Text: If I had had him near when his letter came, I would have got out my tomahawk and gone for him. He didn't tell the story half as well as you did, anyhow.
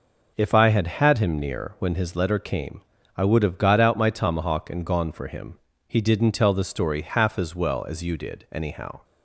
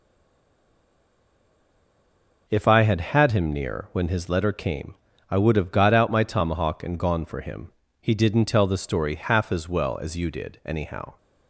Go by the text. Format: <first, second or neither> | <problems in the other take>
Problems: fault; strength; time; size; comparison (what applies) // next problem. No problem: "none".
first | stays silent before the first word; until 2.4 s; 2.4 s long